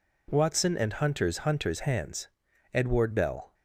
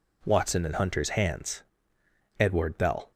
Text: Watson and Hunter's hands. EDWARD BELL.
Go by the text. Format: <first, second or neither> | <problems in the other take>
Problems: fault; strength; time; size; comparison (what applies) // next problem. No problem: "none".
second | says "Hunter's" twice; at 1.3 s